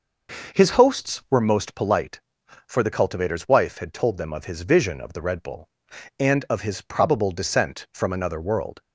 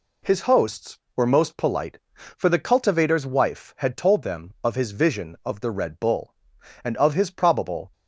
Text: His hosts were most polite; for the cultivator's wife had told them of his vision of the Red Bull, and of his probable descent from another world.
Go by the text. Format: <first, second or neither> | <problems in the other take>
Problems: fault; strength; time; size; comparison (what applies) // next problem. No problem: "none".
first | stops before "descent from another world"; at 7.9 s